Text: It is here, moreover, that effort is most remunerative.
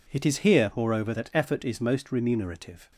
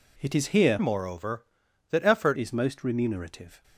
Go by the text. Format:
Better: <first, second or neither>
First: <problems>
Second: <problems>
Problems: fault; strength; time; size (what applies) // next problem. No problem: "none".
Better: first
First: none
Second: changes voice from "moreover" to "effort"; from 0.7 to 2.3 s; 1.6 s long